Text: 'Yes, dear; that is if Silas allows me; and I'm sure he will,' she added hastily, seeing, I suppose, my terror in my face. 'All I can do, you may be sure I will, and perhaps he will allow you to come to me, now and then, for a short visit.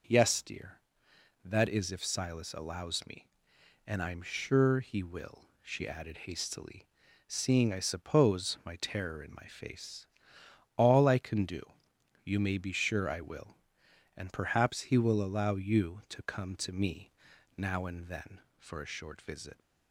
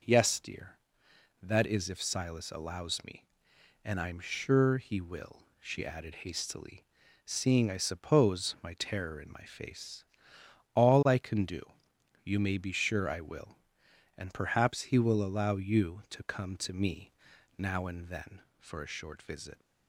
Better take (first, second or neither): neither